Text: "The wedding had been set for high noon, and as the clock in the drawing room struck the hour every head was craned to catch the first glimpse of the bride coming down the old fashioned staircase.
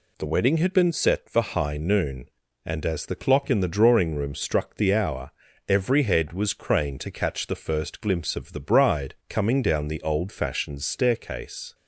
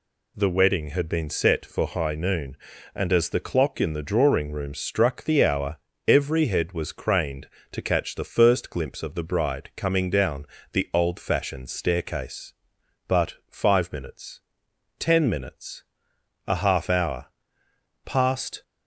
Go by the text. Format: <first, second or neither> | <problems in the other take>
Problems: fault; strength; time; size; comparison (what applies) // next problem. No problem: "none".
first | pauses between "hour" and "every"; slight; at 5.7 s; 0.32 s long; also in the first // pauses between "down" and "the"; slight; at 10.4 s; 0.26 s long // goes on to say "But five minutes ten minutes a half hour passed"; strong; from 13.0 s on; 5.5 s long